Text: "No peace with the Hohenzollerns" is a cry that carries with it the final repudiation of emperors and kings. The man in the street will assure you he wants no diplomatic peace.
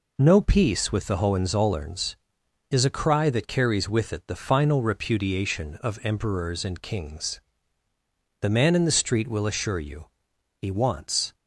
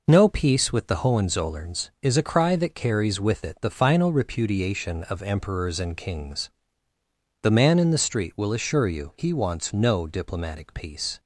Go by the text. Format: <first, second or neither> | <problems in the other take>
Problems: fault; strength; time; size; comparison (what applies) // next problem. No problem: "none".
second | pauses between "you" and "he"; noticeable; at 10.0 s; 0.56 s long // stops before "no diplomatic peace"; at 11.3 s